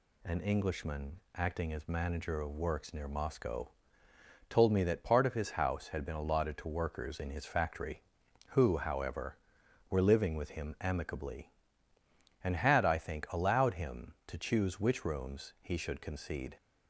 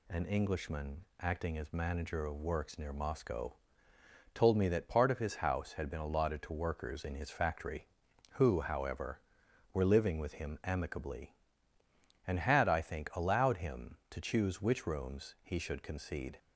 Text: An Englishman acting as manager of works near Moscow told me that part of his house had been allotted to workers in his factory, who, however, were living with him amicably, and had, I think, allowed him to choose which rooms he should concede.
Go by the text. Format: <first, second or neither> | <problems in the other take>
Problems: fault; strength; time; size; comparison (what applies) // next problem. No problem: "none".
neither | pauses between "Moscow" and "told"; noticeable; the same in both